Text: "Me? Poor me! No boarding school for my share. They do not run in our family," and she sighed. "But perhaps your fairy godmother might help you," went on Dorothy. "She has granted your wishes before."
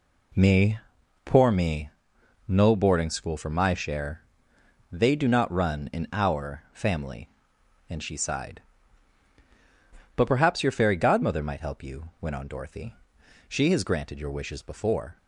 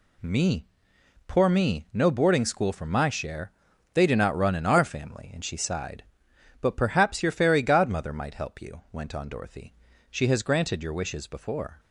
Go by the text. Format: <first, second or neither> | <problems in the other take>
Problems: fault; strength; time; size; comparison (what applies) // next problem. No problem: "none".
neither | none